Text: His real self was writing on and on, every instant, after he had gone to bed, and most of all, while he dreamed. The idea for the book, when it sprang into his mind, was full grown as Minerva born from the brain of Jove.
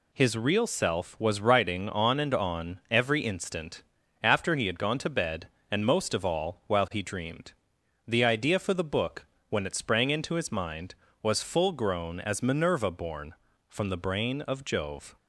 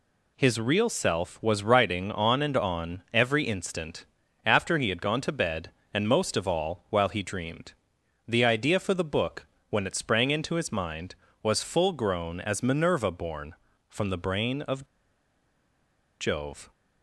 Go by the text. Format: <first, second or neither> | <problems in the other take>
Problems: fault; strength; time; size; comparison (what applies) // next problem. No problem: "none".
first | pauses between "of" and "Jove"; strong; at 14.8 s; 1.3 s long